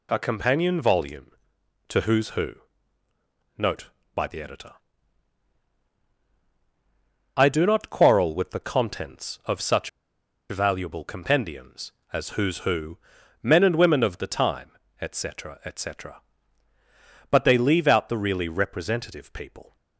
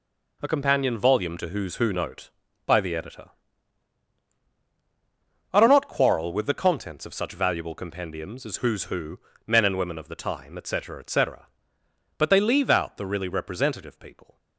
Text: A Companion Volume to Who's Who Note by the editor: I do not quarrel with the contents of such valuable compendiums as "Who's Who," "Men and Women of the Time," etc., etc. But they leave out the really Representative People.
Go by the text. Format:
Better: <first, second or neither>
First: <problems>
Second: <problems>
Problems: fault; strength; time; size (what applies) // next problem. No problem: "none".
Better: second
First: pauses between "Who" and "Note"; at 2.5 s; 1.0 s long // pauses between "such" and "valuable"; noticeable; at 9.8 s; 0.62 s long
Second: none